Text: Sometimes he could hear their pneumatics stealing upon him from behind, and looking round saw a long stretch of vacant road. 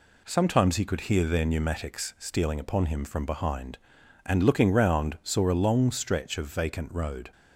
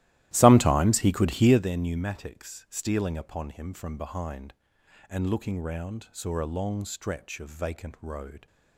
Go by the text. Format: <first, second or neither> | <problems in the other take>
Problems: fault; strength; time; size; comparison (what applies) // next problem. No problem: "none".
first | starts louder than the rest; strong; until 1.7 s; 15 dB